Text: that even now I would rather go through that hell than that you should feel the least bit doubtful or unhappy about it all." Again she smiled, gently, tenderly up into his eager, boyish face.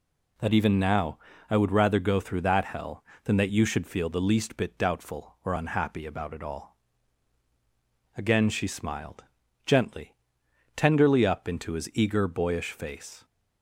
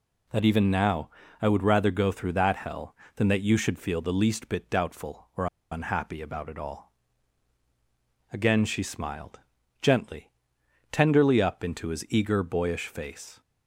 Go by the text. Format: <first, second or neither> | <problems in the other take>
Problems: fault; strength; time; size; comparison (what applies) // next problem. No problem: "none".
first | pauses between "now" and "I"; slight; at 1.0 s; 0.32 s long; slight in the first // pauses between "or" and "unhappy"; slight; at 5.4 s; 0.25 s long